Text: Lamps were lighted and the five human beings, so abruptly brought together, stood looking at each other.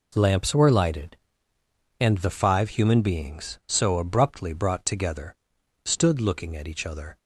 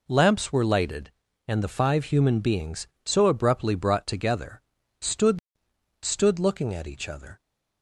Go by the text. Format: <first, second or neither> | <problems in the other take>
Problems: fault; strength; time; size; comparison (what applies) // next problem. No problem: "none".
first | says "stood" twice; at 6.0 s